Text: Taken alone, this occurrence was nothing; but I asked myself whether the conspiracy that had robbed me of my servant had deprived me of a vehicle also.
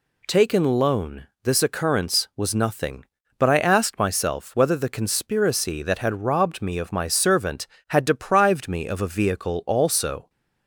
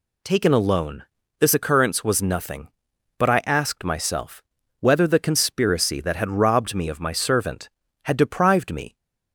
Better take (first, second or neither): first